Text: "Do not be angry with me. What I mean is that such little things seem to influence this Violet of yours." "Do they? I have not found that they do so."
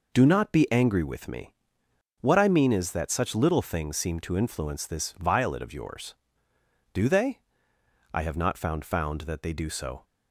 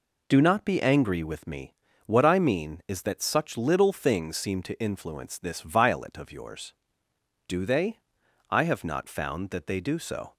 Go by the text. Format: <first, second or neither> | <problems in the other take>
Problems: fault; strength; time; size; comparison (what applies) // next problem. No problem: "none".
second | says "found" twice; at 8.8 s